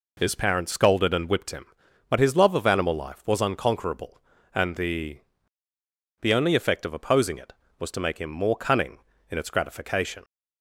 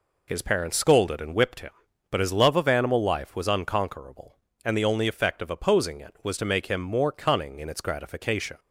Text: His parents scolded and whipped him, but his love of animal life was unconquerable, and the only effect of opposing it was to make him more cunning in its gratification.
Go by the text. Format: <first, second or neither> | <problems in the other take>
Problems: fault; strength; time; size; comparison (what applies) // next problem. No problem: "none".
second | says "the" twice; at 6.2 s